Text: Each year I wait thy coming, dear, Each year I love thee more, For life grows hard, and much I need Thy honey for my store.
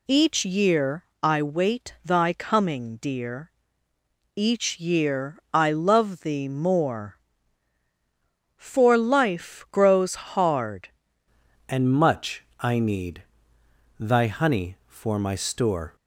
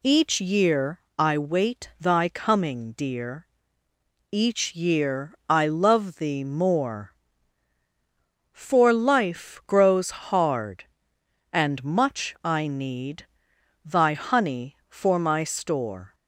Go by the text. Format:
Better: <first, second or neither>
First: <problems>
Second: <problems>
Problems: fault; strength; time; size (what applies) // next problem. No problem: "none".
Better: second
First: pauses between "year" and "I"; slight; at 1.0 s; 0.16 s long // changes voice at "and"; from 11.6 s on; 4.3 s long // pauses between "much" and "I"; slight; at 12.4 s; 0.16 s long // pauses between "need" and "Thy"; noticeable; at 13.2 s; 0.76 s long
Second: pauses between "year" and "I"; slight; at 0.9 s; 0.16 s long // pauses between "need" and "Thy"; noticeable; at 13.2 s; 0.56 s long